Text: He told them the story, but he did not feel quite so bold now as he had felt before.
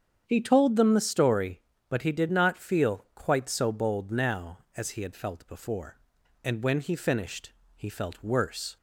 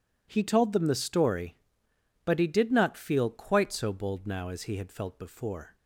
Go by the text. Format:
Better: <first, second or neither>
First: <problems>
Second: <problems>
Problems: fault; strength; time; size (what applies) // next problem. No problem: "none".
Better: second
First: starts louder than the rest; strong; until 1.2 s; 8 dB // goes on to say "And when he finished he felt worse"; strong; from 6.4 s on; 2.3 s long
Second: none